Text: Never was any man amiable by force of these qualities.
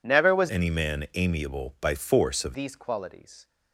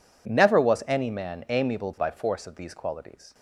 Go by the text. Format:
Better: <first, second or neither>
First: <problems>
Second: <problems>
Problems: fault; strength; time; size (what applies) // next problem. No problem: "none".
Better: second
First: changes voice from "any" to "of"; from 0.4 to 2.5 s; 2.1 s long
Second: none